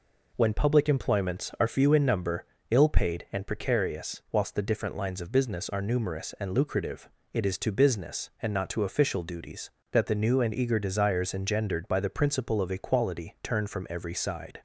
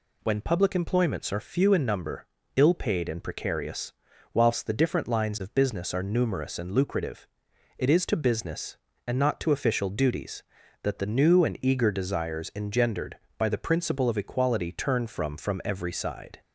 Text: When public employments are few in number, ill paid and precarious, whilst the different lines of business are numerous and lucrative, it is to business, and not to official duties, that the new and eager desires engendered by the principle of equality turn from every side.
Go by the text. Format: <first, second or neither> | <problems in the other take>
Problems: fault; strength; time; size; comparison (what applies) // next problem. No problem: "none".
first | says "from" twice; at 15.3 s